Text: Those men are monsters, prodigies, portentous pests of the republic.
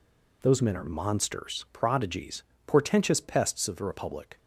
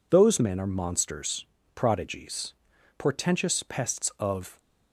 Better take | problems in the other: first | stops before "the republic"; at 4.5 s

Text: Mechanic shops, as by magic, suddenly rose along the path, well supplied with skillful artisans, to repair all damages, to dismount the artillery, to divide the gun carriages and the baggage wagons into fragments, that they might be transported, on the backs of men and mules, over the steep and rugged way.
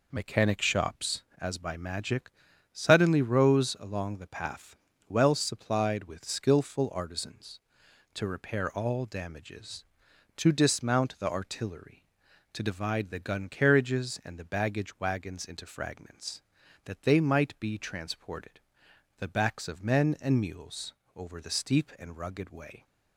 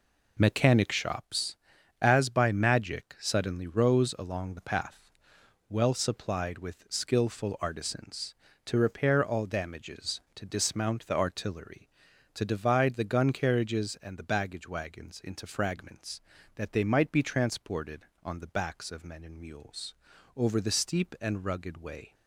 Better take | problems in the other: second | skips "on"; at 18.8 s

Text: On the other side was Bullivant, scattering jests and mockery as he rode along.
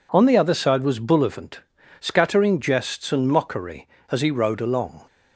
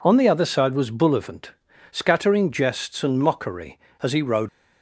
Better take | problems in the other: first | stops before "along"; at 4.4 s

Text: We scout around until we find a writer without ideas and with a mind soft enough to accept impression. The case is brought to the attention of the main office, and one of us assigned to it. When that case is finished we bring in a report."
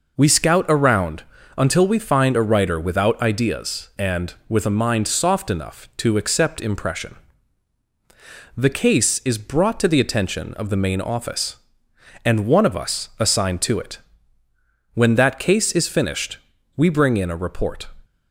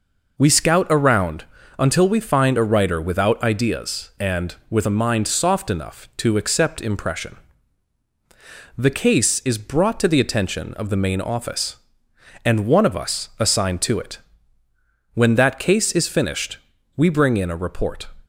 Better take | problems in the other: neither | pauses between "around" and "until"; slight; the same in both // pauses between "finished" and "we"; the same in both

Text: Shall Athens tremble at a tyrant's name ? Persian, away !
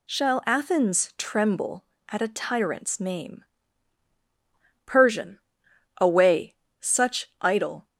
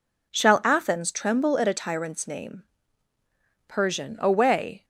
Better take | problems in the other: second | goes on to say "such idle"; noticeable; from 6.7 s on; 1.0 s long

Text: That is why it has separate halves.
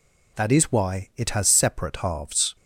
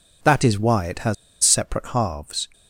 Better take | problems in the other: first | pauses between "has" and "separate"; slight; at 1.1 s; 0.29 s long

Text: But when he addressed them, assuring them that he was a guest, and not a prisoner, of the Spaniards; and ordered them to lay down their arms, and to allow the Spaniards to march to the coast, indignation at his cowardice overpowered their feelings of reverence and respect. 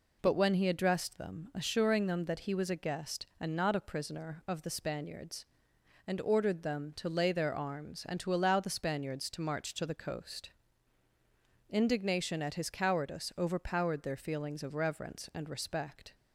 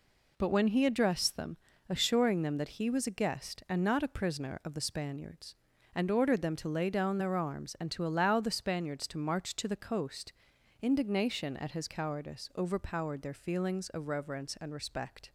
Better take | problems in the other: second | skips "down"; at 7.2 s

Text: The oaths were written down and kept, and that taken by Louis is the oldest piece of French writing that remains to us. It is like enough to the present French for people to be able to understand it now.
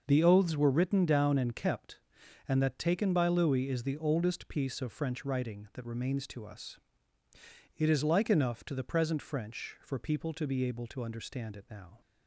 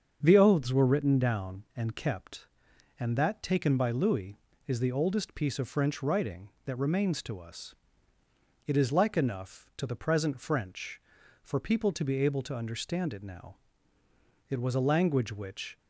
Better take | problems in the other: first | starts louder than the rest; until 1.2 s; 7 dB; noticeable in the first // goes on to say "It was a language which"; noticeable; from 14.4 s on; 1.3 s long

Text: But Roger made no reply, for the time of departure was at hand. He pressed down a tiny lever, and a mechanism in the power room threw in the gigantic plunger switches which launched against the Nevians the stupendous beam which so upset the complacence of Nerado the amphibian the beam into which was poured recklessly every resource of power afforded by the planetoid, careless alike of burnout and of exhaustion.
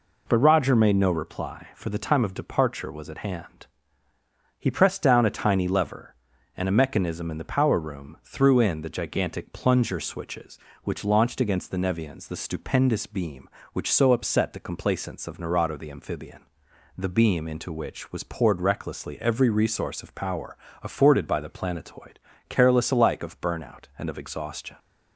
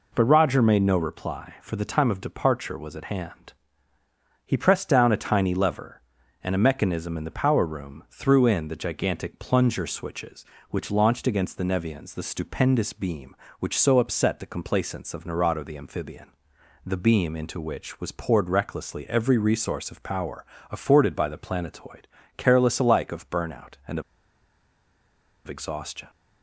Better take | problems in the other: first | pauses between "amphibian" and "the"; noticeable; at 16.2 s; 0.56 s long; noticeable in the first // pauses between "power" and "afforded"; slight; at 20.4 s; 0.26 s long; slight in the first // pauses between "of" and "exhaustion"; strong; at 24.0 s; 1.4 s long

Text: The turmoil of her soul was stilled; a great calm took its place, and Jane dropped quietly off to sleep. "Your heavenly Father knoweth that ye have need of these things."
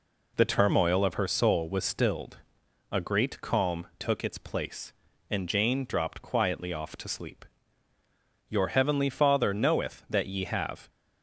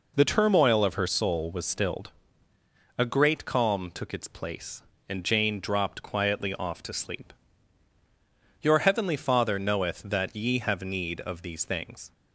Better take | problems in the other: second | stops before "need of these things"; at 10.8 s

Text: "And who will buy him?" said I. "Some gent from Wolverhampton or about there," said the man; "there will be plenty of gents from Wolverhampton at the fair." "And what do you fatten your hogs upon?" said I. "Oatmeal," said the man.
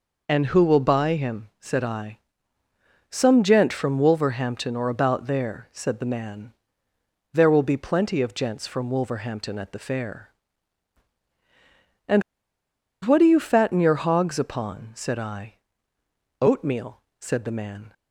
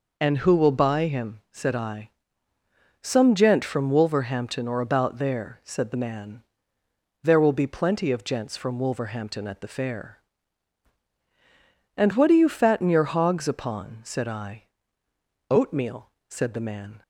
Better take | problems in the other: second | pauses between "And" and "what"; noticeable; at 12.2 s; 0.82 s long

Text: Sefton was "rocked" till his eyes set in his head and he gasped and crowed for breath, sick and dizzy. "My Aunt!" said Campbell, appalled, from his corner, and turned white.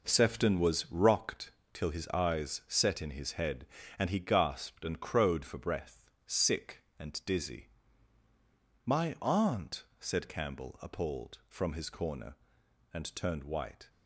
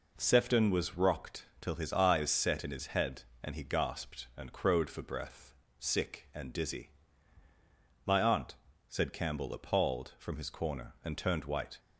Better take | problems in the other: second | gets quieter; strong; throughout; 9 dB // pauses between "rocked" and "till"; slight; at 1.4 s; 0.24 s long

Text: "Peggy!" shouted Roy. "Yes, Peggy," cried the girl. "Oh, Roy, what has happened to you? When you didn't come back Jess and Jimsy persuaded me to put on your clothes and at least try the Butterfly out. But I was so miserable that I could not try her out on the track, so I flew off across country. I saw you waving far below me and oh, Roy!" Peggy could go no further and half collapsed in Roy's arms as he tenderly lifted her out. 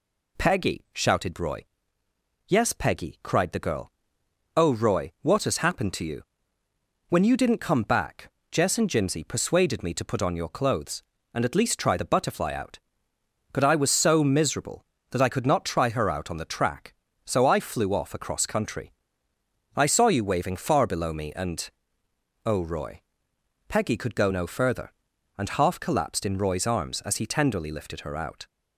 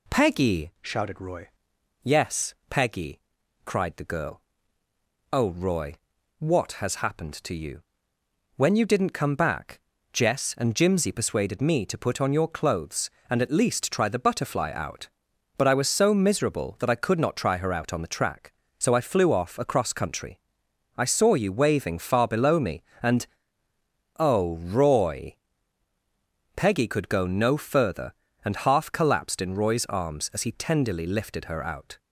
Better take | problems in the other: first | changes voice from "shouted" to "Roy"; from 0.8 to 1.4 s; 0.6 s long // pauses between "back" and "Jess"; slight; at 9.8 s; 0.34 s long; slight in the first // pauses between "and" and "oh"; noticeable; at 23.2 s; 0.92 s long; noticeable in the first

